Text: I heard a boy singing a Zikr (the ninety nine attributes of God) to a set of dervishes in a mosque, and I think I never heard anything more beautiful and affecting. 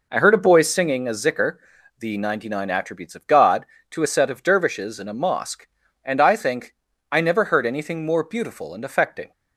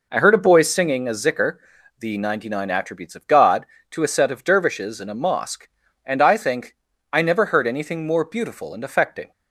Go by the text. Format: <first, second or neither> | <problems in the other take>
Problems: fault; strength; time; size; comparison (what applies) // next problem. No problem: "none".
neither | pauses between "think" and "I"; slight; the same in both